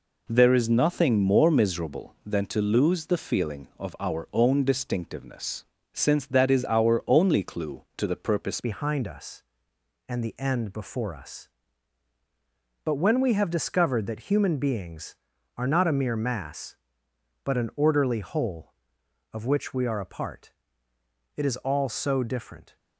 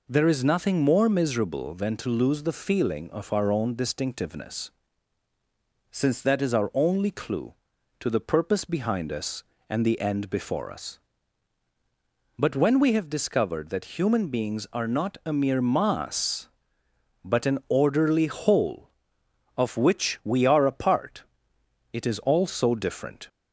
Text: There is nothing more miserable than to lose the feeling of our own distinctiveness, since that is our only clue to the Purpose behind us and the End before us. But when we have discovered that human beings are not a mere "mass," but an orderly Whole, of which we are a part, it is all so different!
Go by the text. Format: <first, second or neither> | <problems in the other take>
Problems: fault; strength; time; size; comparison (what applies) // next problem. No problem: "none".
second | changes voice at "behind"; from 8.6 s on; 14.1 s long